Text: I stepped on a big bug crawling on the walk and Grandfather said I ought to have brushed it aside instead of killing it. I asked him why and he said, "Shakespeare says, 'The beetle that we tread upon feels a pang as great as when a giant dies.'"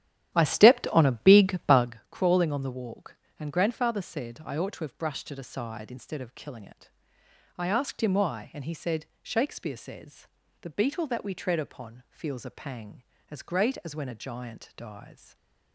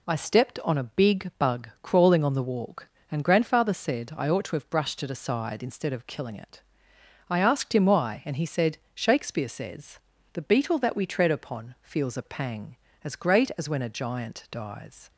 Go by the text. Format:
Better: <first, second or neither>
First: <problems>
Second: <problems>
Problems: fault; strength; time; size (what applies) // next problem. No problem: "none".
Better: second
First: starts louder than the rest; strong; until 2.0 s; 11.5 dB // stays silent after the last word; slight; from 15.1 s on; 0.6 s long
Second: none